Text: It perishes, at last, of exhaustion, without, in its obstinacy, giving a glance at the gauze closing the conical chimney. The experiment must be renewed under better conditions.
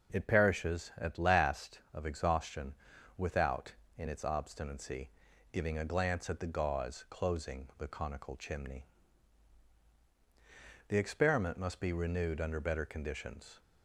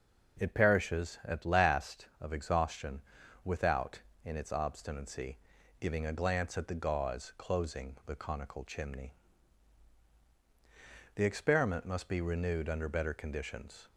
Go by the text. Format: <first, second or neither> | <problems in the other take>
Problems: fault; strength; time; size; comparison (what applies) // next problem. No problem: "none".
neither | none